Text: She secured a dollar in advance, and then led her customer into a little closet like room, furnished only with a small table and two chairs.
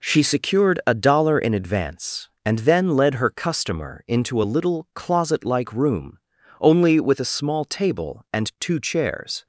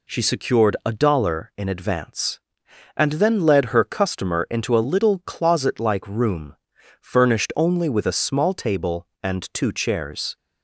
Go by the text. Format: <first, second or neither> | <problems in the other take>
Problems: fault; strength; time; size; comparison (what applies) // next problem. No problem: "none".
second | skips "furnished"; at 6.3 s